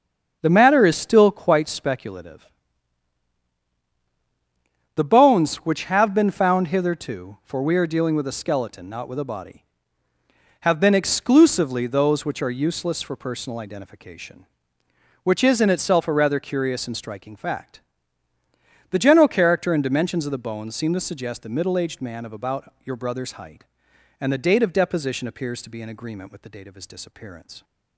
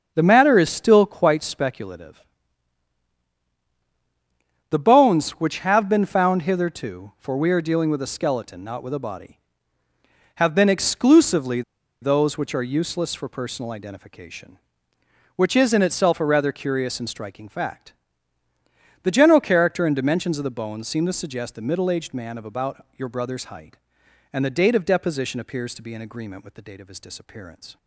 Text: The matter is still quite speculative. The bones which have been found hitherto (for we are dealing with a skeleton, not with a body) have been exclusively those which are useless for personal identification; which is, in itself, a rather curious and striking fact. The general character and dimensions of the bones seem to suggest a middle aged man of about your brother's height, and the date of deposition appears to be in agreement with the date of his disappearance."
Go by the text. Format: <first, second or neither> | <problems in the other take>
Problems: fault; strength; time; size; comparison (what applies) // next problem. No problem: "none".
first | starts louder than the rest; until 1.1 s; 6.5 dB; also in the first // pauses between "exclusively" and "those"; at 11.6 s; 0.40 s long